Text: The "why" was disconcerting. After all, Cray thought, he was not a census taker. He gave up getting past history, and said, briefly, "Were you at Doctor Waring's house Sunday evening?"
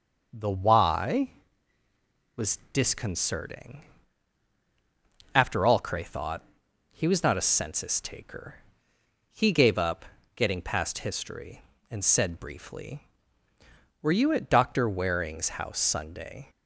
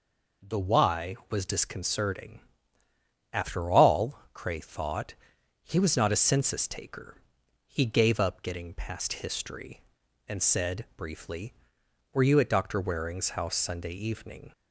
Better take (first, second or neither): second